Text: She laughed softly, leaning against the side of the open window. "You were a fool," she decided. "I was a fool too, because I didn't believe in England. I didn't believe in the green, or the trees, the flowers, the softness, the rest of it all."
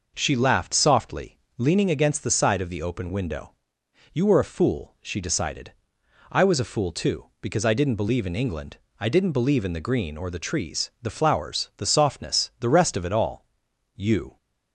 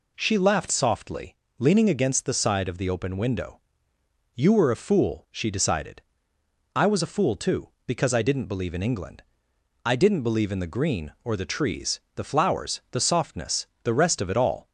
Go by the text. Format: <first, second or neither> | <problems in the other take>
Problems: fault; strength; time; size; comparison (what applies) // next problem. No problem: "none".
second | goes on to say "You"; slight; from 13.9 s on; 0.40 s long